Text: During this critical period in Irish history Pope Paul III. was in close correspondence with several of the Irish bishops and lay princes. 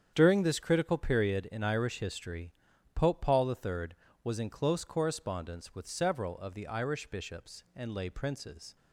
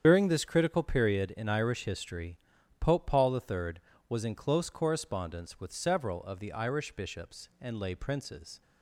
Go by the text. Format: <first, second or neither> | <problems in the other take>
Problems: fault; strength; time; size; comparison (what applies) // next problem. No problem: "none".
first | loses the start of "During"; at 0.0 s; 45 ms // starts louder than the rest; strong; until 1.0 s; 8.5 dB; strong in the first // pauses between "history" and "Pope"; at 2.3 s; 0.42 s long; also in the first